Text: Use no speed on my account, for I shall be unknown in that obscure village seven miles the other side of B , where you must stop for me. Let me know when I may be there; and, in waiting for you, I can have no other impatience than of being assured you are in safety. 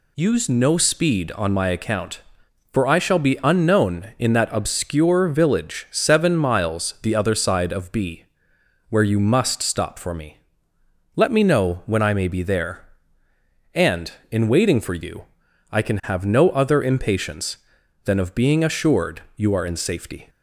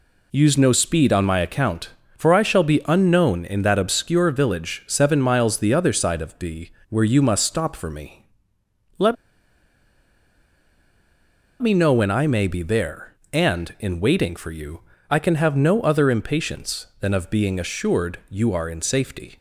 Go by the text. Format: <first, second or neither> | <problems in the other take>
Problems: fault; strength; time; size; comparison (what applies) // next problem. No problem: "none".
first | pauses between "Let" and "me"; strong; at 9.1 s; 2.4 s long